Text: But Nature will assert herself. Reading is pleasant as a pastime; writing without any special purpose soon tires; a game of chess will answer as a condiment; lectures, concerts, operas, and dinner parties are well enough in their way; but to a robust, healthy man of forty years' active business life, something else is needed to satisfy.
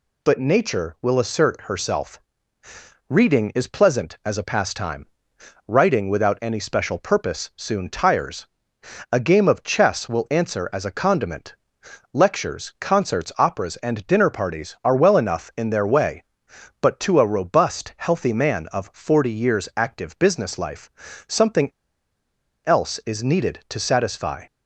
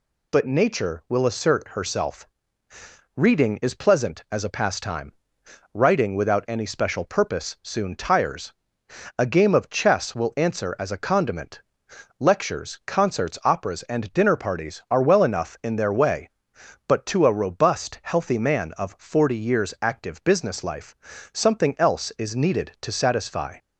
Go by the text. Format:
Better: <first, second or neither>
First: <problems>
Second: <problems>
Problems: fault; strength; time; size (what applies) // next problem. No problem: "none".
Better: second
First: pauses between "something" and "else"; noticeable; at 21.6 s; 0.95 s long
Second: none